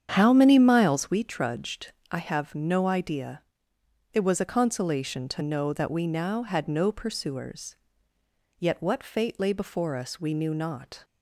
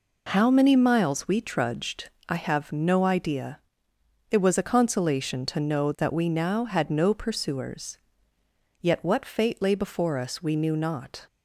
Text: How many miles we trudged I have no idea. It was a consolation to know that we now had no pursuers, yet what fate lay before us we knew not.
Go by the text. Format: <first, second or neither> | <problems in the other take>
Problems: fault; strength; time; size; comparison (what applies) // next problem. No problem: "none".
second | starts louder than the rest; strong; until 1.2 s; 8.5 dB // pauses between "trudged" and "I"; slight; at 1.9 s; 0.18 s long; slight in the second